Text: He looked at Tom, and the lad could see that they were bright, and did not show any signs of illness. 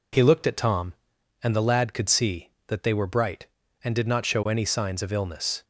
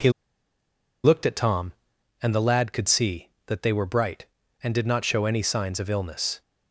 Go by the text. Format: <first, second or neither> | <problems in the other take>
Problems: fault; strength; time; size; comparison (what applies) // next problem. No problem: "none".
first | pauses between "He" and "looked"; noticeable; at 0.0 s; 0.94 s long